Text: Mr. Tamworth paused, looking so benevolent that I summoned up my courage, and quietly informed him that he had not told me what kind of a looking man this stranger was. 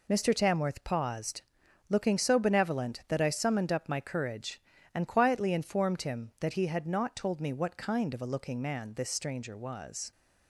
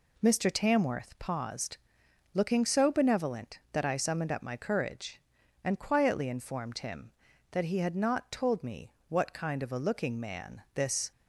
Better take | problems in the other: first | pauses between "me" and "what"; slight; at 8.8 s; 0.20 s long // stops before "stranger was"; at 11.1 s

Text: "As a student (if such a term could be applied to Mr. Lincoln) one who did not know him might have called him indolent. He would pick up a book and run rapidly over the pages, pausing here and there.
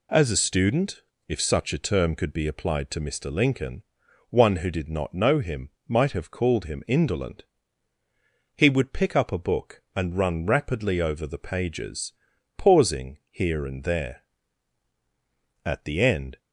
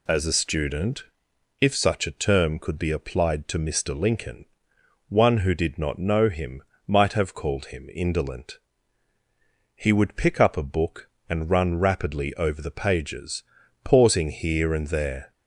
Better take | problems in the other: second | pauses between "him" and "might"; slight; at 5.7 s; 0.16 s long; slight in the second // goes on to say "At the end"; noticeable; from 15.6 s on; 0.74 s long

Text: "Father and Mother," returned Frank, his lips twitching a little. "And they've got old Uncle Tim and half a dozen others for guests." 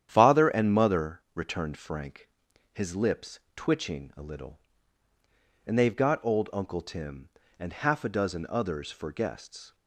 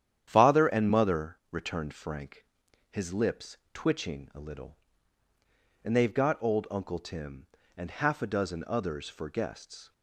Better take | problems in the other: neither | starts louder than the rest; strong; the same in both

